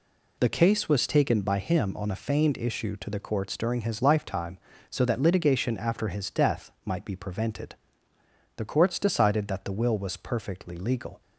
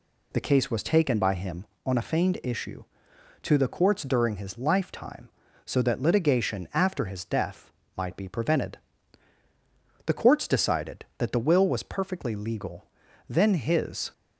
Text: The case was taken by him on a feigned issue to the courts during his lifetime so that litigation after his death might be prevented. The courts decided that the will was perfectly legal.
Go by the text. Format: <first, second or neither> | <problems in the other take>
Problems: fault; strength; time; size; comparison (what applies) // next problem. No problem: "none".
first | pauses between "death" and "might"; slight; at 7.7 s; 0.24 s long // goes on to say "Then his"; noticeable; from 13.2 s on; 0.84 s long